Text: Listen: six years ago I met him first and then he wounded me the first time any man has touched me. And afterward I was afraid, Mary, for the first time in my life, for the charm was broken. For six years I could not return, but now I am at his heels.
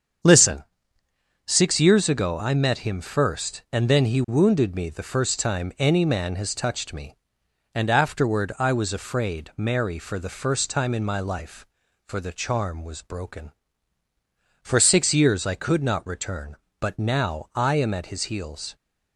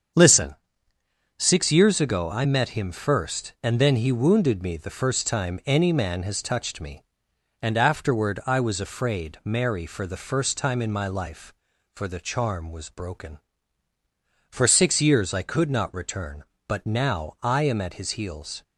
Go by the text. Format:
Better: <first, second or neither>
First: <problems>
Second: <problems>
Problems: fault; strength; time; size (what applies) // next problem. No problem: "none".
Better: neither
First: starts louder than the rest; strong; until 2.1 s; 7.5 dB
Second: starts louder than the rest; strong; until 2.0 s; 7.5 dB